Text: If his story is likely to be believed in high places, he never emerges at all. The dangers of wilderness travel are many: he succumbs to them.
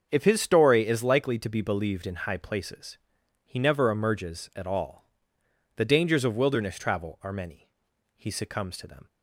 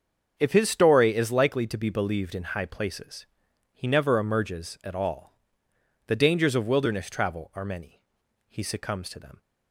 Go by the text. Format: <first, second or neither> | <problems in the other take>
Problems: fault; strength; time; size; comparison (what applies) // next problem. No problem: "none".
neither | starts louder than the rest; the same in both